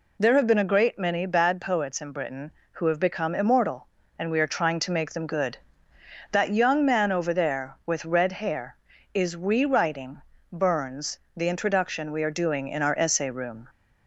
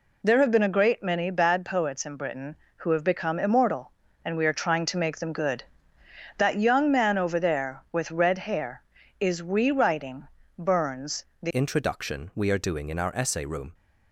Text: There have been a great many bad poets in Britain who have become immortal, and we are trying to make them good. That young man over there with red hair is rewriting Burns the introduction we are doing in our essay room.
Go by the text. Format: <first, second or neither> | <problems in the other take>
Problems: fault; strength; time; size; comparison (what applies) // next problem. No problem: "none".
first | pauses between "rewriting" and "Burns"; slight; at 10.2 s; 0.32 s long; slight in the first // pauses between "Burns" and "the"; slight; at 11.2 s; 0.16 s long; slight in the first // changes voice at "introduction"; from 11.5 s on; 2.2 s long